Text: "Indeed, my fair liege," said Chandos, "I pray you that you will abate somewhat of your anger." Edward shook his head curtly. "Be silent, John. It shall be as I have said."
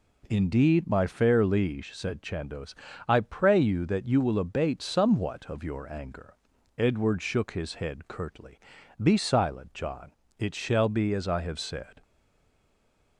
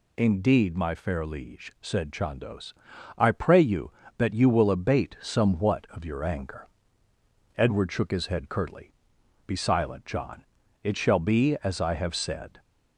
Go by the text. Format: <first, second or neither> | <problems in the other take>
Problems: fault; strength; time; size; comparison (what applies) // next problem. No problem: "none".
second | stays silent after the last word; noticeable; from 12.0 s on; 1.1 s long